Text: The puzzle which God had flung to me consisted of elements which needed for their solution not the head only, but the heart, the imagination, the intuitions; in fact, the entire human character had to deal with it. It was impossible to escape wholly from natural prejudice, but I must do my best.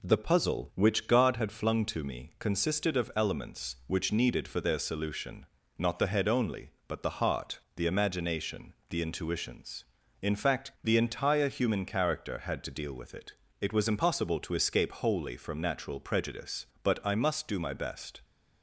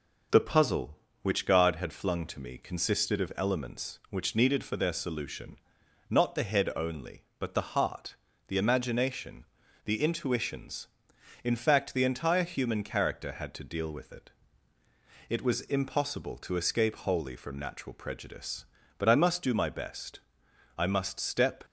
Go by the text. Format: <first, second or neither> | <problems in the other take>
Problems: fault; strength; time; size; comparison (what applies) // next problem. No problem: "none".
first | pauses between "solution" and "not"; noticeable; at 5.5 s; 0.56 s long; slight in the first // goes on to say "I must step"; noticeable; from 20.7 s on; 0.88 s long